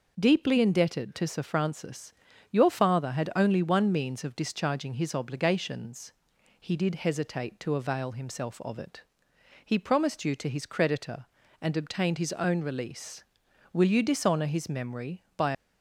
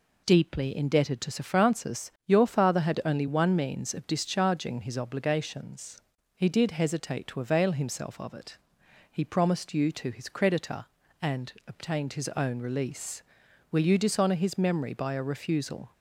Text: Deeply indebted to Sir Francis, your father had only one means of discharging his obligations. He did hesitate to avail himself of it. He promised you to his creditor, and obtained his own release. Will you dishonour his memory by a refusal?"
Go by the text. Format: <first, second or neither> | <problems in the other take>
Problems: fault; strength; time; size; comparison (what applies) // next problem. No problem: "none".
second | stops before "a refusal"; at 15.5 s